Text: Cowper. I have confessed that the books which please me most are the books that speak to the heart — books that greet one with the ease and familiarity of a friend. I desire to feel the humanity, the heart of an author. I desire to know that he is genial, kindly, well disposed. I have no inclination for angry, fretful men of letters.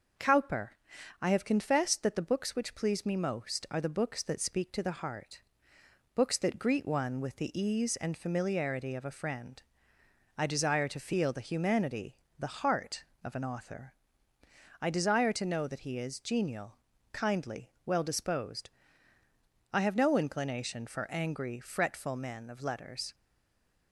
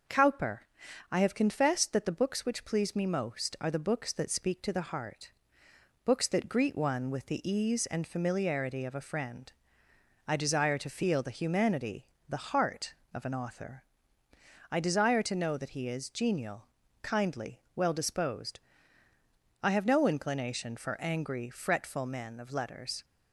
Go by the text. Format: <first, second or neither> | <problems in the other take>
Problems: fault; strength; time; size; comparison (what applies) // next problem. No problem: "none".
second | starts louder than the rest; noticeable; until 1.6 s; 6 dB; noticeable in the second // stays silent after the last word; slight; from 23.1 s on; 0.8 s long